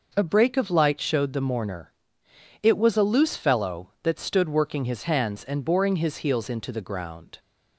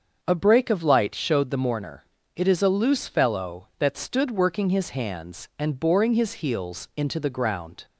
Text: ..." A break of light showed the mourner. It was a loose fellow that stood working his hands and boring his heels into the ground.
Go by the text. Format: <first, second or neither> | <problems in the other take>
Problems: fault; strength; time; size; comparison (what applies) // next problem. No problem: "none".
first | starts louder than the rest; until 1.2 s; 6.5 dB // says "is" for "was"; at 2.4 s